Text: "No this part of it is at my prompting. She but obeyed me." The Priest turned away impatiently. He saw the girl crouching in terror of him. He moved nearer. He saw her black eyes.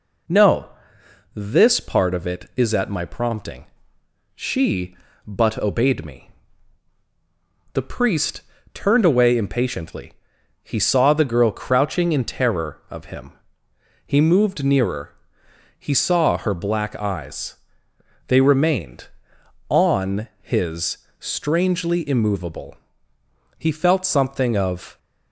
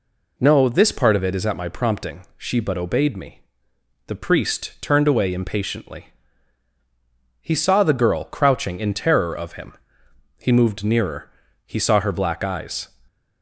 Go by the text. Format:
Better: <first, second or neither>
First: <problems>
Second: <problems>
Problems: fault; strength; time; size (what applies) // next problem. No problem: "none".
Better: second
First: pauses between "No" and "this"; noticeable; at 0.6 s; 0.68 s long // pauses between "Priest" and "turned"; slight; at 8.3 s; 0.34 s long // goes on to say "They remained on his strangely immovable He felt something of"; strong; from 18.2 s on; 6.7 s long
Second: none